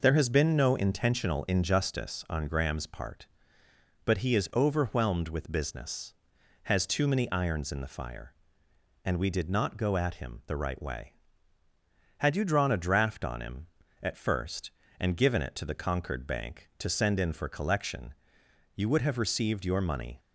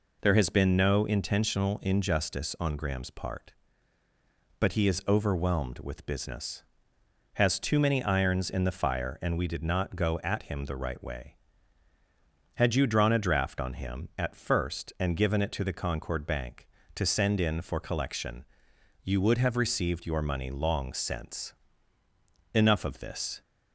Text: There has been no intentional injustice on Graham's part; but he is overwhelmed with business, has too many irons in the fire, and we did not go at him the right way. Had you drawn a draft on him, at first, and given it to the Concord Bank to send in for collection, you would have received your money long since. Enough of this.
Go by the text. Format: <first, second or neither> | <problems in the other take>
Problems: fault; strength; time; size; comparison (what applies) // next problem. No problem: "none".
second | stops before "long since Enough of this"; at 20.1 s